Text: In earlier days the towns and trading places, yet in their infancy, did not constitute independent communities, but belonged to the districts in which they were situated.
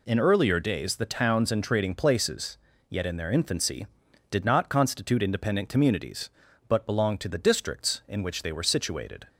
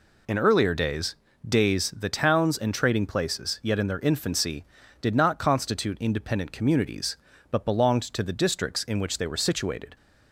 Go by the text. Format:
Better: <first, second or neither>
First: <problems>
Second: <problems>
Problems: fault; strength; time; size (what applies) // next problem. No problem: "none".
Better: first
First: none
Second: says "days" twice; at 1.4 s